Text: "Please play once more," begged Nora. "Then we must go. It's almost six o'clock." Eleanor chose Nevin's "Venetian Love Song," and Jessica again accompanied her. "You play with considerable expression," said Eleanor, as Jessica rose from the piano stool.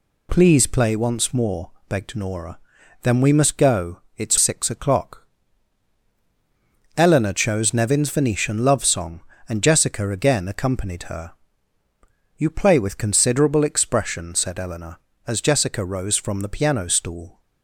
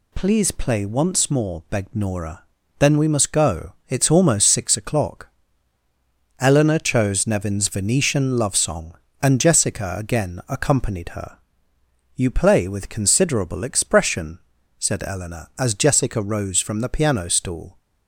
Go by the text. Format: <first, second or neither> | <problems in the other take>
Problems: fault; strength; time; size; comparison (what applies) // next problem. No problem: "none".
second | skips "almost"; at 4.3 s